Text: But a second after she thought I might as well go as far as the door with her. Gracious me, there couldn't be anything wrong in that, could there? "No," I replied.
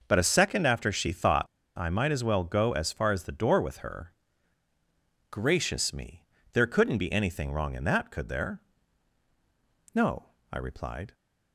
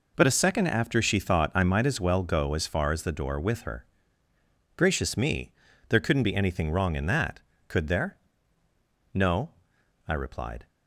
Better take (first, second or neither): second